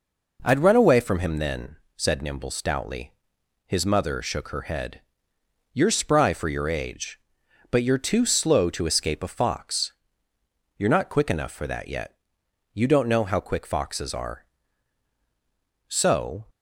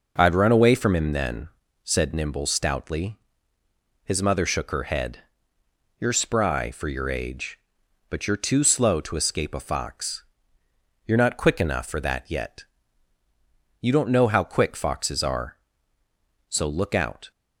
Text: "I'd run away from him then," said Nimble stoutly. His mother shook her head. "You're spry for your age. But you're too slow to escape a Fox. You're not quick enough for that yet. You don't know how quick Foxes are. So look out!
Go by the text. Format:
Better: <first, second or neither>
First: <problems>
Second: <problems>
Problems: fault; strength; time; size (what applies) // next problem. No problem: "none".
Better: second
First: stops before "look out"; at 16.4 s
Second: none